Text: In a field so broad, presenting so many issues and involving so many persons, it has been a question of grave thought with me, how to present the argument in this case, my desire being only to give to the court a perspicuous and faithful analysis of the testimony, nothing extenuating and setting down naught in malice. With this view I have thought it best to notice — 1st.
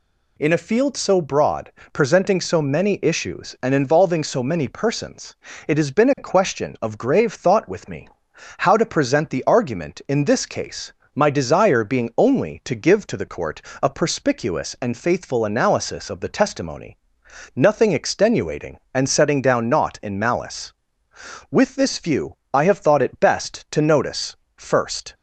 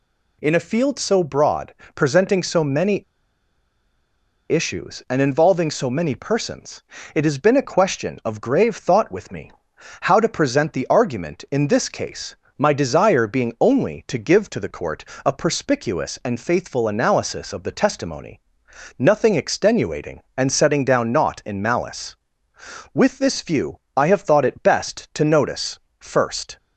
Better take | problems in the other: first | pauses between "many" and "issues"; strong; at 3.0 s; 1.4 s long // pauses between "court" and "a"; slight; at 15.0 s; 0.22 s long; slight in the first

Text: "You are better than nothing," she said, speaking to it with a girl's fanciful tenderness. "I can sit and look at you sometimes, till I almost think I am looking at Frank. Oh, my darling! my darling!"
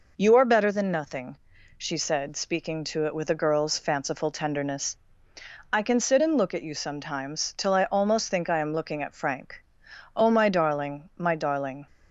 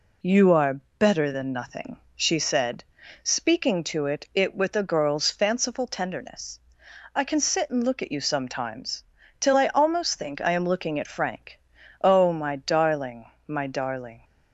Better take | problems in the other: first | pauses between "are" and "better"; slight; at 0.7 s; 0.20 s long // says "it" twice; at 4.3 s

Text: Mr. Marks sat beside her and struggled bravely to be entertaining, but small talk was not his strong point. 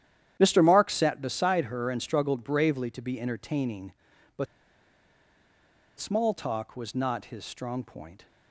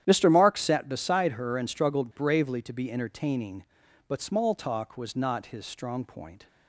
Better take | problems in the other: second | starts louder than the rest; strong; until 1.4 s; 10.5 dB; strong in the second // pauses between "but" and "small"; strong; at 4.4 s; 1.5 s long

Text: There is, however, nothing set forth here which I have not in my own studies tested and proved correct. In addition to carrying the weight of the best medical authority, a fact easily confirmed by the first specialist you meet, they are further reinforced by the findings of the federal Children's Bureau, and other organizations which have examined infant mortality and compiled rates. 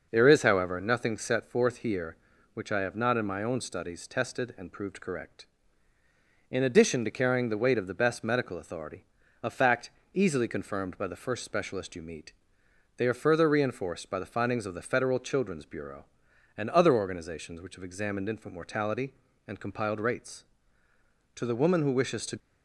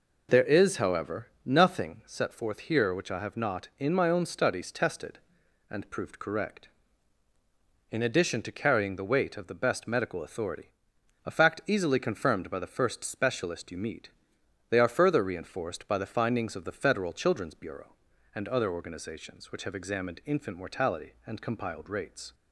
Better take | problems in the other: second | pauses between "fact" and "easily"; slight; at 9.9 s; 0.24 s long // goes on to say "To the woman who wishes to"; noticeable; from 21.3 s on; 1.0 s long

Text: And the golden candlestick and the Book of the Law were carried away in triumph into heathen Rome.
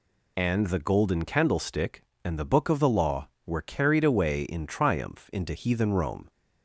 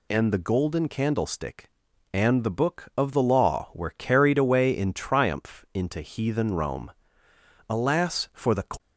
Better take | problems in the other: first | goes on to say "Alas for the"; noticeable; from 7.6 s on; 0.96 s long

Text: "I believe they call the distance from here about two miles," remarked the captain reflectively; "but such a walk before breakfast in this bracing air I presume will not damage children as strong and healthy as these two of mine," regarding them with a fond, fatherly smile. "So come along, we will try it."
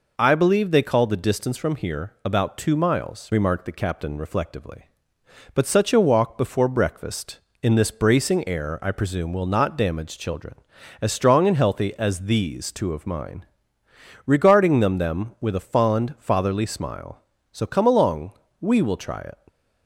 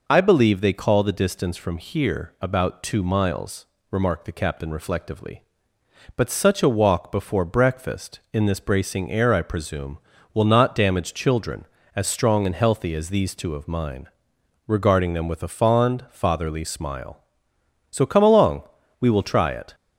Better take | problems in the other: second | says "them" twice; at 14.9 s

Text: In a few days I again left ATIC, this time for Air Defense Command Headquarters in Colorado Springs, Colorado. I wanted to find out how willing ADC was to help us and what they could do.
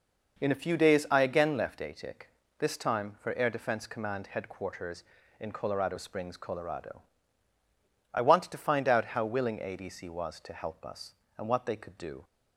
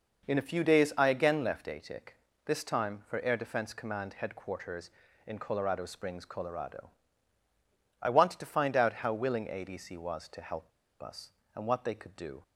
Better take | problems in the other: first | pauses between "help" and "us"; slight; at 10.7 s; 0.31 s long

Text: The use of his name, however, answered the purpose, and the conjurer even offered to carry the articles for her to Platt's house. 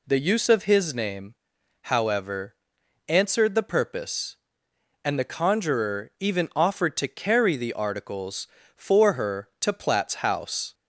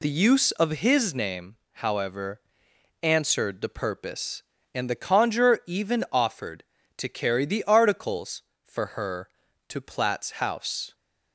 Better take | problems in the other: neither | none

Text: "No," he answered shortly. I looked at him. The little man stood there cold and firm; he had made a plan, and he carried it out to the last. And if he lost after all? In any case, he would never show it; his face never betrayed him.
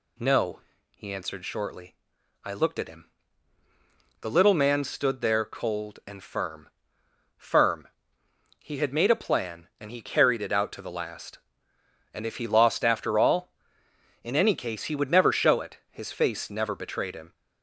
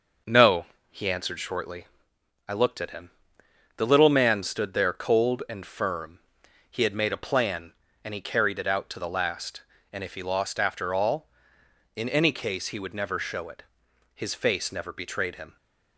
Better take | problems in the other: second | says "firm" twice; at 7.3 s

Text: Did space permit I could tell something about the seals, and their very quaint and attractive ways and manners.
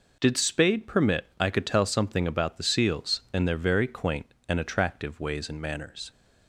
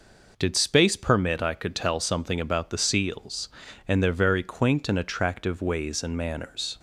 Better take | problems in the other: second | says "spade" for "space"; at 0.3 s

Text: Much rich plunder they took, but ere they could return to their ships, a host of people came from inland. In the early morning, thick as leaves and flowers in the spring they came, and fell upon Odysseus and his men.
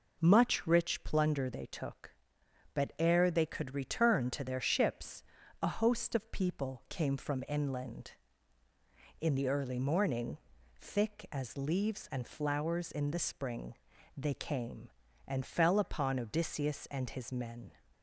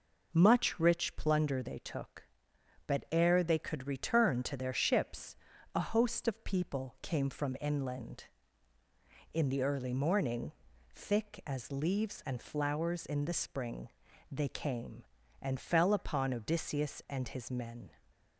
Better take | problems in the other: neither | pauses between "spring" and "they"; the same in both

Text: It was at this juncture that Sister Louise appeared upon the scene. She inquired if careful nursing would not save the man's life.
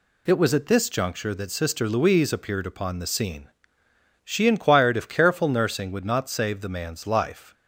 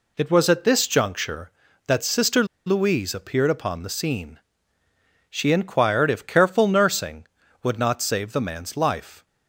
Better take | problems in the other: first | pauses between "Sister" and "Louise"; slight; at 2.4 s; 0.21 s long

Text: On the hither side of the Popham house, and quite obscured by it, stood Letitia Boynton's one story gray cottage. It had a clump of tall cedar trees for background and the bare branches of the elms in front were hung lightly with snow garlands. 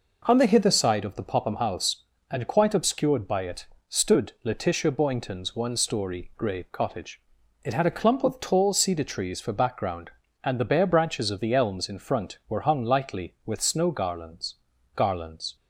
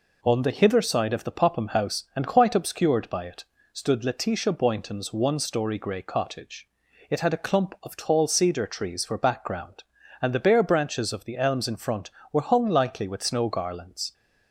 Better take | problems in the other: second | says "garlands" twice; at 14.9 s

